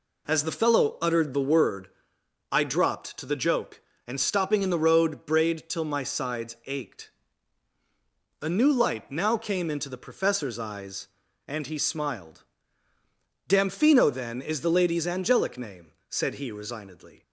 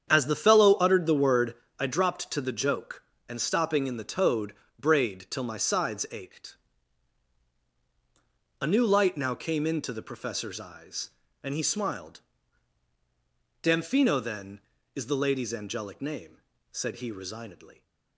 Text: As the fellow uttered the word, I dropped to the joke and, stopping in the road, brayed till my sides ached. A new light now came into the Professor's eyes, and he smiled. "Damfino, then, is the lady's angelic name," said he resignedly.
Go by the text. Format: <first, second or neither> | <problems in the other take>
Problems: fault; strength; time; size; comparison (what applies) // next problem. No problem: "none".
first | starts louder than the rest; strong; until 1.1 s; 8 dB // says "toad" for "road"; at 4.0 s